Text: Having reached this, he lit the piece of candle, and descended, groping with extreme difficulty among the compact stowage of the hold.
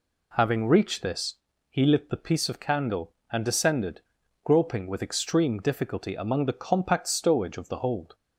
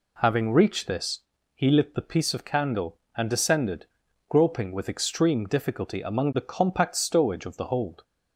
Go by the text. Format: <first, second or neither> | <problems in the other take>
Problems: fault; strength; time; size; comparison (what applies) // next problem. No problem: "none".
neither | none